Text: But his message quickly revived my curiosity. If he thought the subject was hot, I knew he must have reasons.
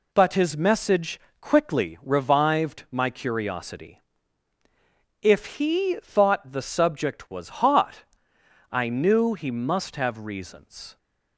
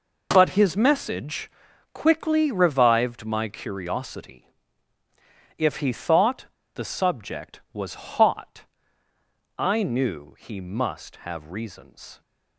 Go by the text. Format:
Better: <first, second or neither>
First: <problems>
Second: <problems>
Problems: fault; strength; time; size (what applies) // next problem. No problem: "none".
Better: first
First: pauses between "message" and "quickly"; slight; at 1.1 s; 0.20 s long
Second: pauses between "message" and "quickly"; at 1.4 s; 0.42 s long // pauses between "thought" and "the"; slight; at 6.4 s; 0.29 s long